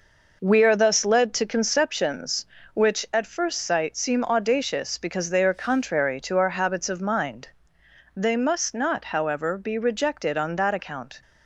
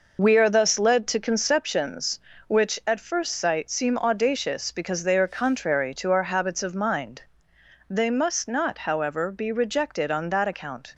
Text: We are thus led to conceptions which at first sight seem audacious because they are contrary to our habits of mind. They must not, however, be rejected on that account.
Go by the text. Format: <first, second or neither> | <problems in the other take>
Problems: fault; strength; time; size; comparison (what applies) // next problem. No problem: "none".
first | loses the start of "We"; at 0.1 s; 45 ms